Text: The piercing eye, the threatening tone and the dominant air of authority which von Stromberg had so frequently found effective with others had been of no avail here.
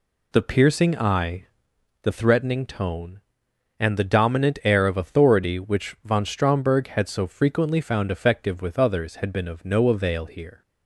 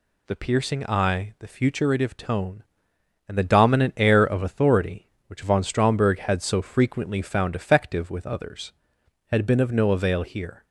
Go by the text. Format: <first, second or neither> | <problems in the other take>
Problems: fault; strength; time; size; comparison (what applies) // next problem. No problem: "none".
first | says "futuritive" for "threatening"; at 1.4 s